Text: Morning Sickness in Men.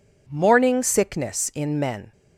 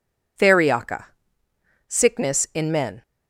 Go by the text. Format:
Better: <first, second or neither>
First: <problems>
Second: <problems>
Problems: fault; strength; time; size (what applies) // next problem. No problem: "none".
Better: first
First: none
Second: says "Theriaca" for "Morning"; at 0.3 s